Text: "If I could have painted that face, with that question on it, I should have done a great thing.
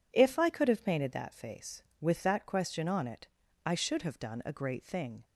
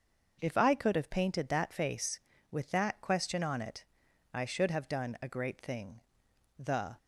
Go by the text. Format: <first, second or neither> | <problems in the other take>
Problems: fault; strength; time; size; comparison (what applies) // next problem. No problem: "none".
first | starts louder than the rest; until 1.4 s; 6.5 dB // goes on to say "The"; slight; from 6.5 s on; 0.40 s long